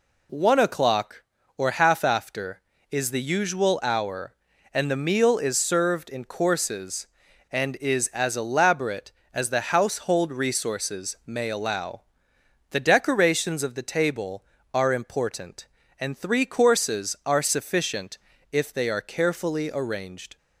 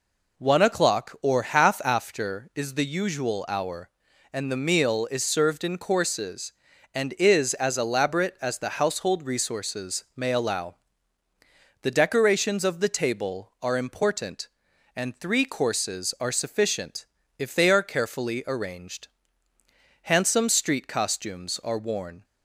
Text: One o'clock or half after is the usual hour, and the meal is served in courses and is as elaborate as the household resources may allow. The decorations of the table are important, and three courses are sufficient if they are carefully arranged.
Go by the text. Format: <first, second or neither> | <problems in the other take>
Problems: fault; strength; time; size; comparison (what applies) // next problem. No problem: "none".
first | pauses between "sufficient" and "if"; slight; at 17.0 s; 0.32 s long; slight in the first // goes on to say "Handsome street costumes are worn"; strong; from 20.0 s on; 2.2 s long